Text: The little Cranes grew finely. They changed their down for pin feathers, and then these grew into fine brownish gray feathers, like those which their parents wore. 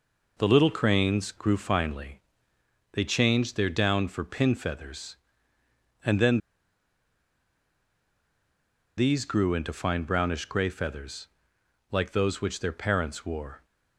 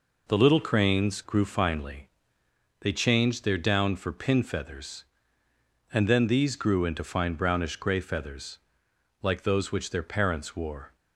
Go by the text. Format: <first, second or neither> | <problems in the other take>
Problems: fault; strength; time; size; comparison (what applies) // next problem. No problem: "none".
second | pauses between "then" and "these"; strong; at 6.3 s; 2.5 s long